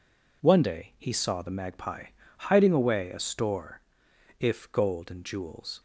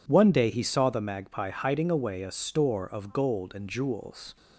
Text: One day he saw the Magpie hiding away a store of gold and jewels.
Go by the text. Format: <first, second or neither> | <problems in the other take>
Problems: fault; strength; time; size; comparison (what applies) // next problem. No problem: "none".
second | pauses between "Magpie" and "hiding"; slight; at 2.0 s; 0.28 s long // says "if" for "of"; at 4.3 s